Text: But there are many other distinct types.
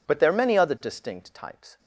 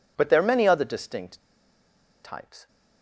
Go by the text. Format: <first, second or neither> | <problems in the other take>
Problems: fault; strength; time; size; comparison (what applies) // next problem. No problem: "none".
first | pauses between "distinct" and "types"; noticeable; at 1.4 s; 0.82 s long